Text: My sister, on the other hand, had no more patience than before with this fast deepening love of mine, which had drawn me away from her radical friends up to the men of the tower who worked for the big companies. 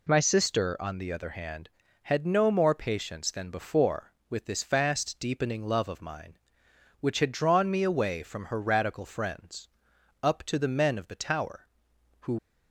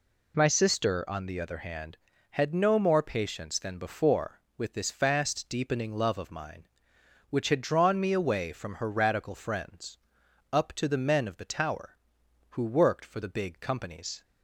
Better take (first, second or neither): second